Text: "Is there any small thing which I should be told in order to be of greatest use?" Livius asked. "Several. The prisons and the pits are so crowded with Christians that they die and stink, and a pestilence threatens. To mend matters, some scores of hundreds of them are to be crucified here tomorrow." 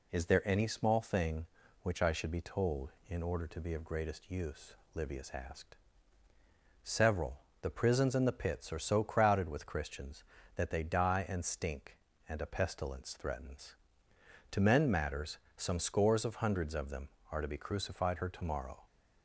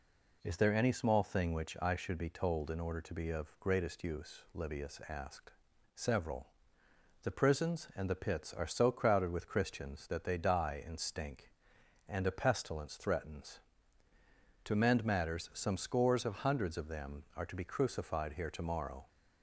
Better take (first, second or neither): second